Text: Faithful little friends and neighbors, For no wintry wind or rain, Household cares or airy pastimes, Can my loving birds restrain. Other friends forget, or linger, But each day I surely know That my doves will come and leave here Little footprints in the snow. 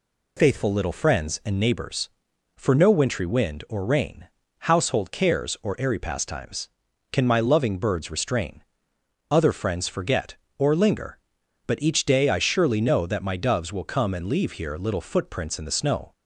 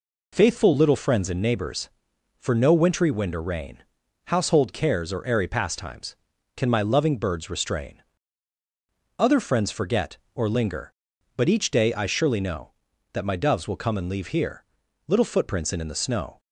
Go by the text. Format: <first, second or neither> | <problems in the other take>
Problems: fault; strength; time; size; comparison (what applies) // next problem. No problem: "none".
first | pauses between "here" and "Little"; at 14.6 s; 0.42 s long // says "in" twice; at 15.7 s